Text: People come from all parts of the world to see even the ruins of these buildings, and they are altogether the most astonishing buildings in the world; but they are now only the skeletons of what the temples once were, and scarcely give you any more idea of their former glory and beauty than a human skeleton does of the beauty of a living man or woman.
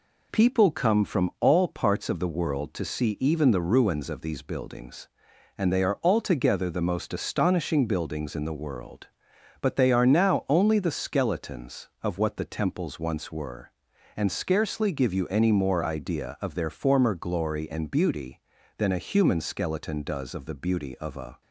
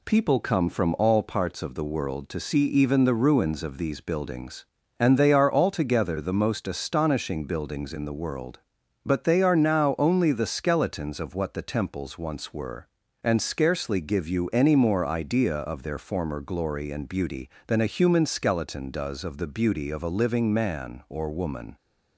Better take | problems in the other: second | stops before "living man or woman"; at 21.4 s

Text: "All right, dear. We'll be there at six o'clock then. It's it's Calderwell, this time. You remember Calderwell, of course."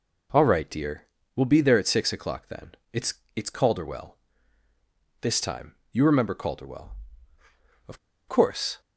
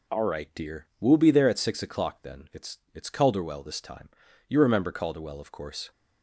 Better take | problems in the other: second | pauses between "It's" and "it's"; slight; at 3.1 s; 0.20 s long; slight in the second // pauses between "of" and "course"; slight; at 7.9 s; 0.29 s long

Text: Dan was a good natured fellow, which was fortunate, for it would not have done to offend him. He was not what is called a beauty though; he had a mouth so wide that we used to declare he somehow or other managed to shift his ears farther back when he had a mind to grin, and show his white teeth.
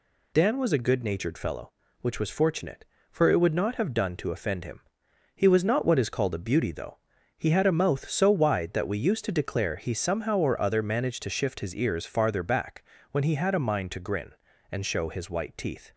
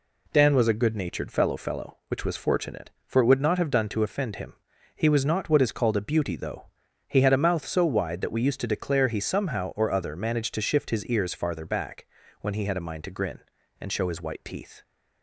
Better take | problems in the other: first | says "fellow" twice; at 1.5 s // pauses between "back" and "when"; slight; at 12.0 s; 0.34 s long; slight in the first

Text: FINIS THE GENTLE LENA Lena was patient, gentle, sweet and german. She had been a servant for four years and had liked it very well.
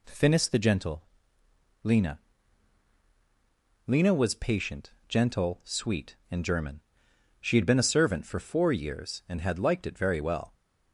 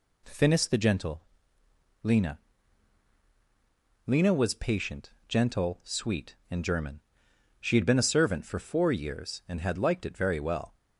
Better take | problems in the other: neither | pauses between "GENTLE" and "LENA"; noticeable; the same in both // pauses between "LENA" and "Lena"; strong; the same in both

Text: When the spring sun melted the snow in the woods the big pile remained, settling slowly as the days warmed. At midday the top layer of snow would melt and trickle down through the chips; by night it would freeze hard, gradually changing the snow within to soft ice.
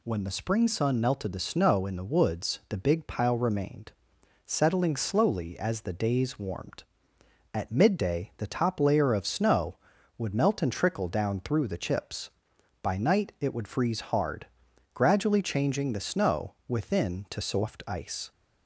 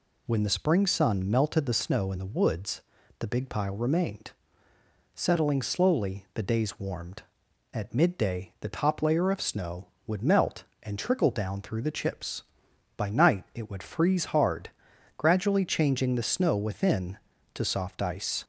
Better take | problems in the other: first | pauses between "woods" and "the"; at 2.8 s; 0.38 s long // skips "as"; at 6.2 s

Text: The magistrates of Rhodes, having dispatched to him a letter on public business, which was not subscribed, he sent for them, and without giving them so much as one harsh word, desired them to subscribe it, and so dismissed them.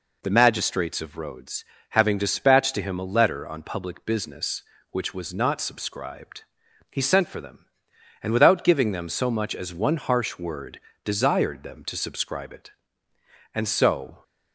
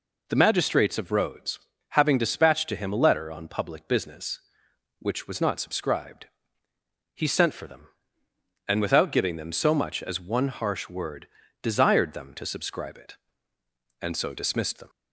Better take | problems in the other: second | stops before "dismissed them"; at 14.2 s

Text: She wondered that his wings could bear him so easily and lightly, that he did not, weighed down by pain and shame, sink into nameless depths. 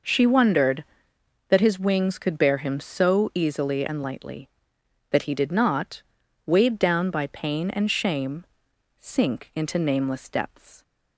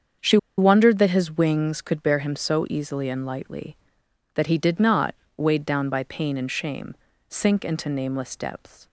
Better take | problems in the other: first | starts louder than the rest; strong; until 1.4 s; 7 dB // pauses between "She" and "wondered"; slight; at 0.3 s; 0.21 s long

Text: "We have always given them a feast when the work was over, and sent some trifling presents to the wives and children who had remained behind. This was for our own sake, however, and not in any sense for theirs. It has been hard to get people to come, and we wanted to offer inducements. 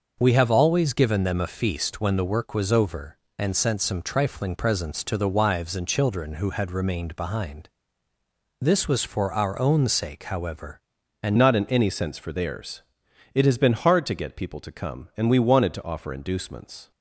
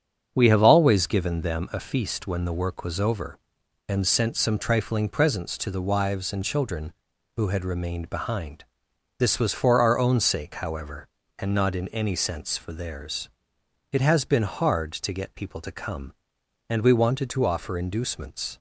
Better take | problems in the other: second | starts louder than the rest; noticeable; until 1.1 s; 6 dB; strong in the second // changes voice at "not"; from 11.3 s on; 5.6 s long

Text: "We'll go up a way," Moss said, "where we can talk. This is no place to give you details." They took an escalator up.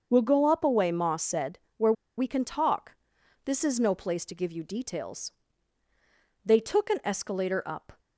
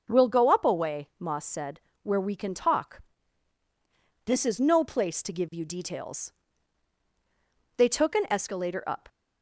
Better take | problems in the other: second | starts louder than the rest; until 1.1 s; 6.5 dB // pauses between "where" and "we"; slight; at 1.9 s; 0.25 s long

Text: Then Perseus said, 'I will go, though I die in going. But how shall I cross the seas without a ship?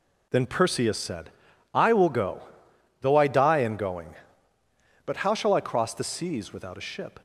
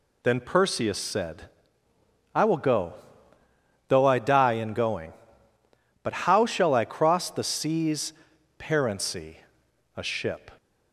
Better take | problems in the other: first | says "parency" for "without"; at 8.5 s

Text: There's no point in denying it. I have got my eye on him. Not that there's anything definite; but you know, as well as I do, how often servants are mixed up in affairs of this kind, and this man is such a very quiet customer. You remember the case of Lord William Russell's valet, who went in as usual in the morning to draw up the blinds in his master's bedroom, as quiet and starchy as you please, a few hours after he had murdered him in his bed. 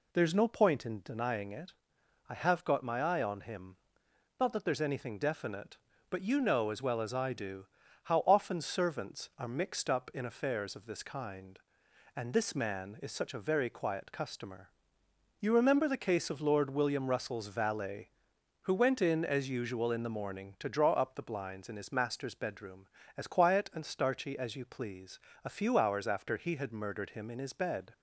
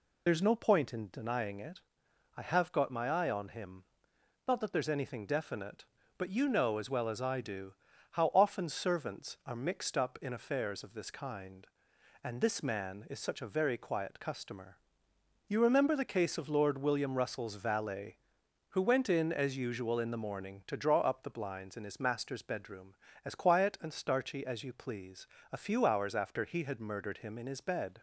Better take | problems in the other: first | loses the start of "There's"; at 0.2 s; 60 ms

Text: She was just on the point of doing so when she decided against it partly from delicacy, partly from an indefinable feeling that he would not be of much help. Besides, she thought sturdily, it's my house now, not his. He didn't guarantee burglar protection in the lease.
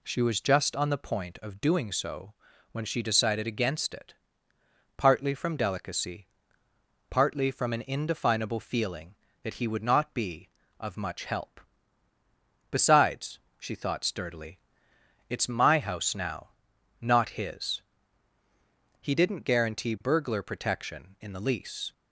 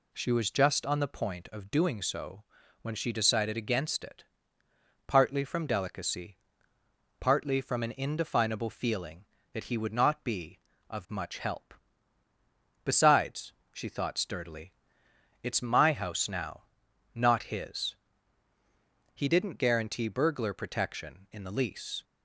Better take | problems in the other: neither | pauses between "so" and "when"; the same in both // pauses between "it" and "partly"; noticeable; the same in both

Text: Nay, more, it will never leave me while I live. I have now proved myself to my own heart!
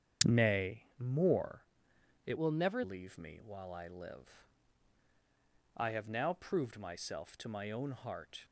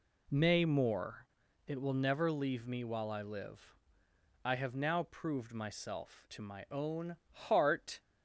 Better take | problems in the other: second | starts louder than the rest; strong; until 1.3 s; 7.5 dB // changes voice from "will" to "never"; from 2.3 to 2.8 s; 0.5 s long

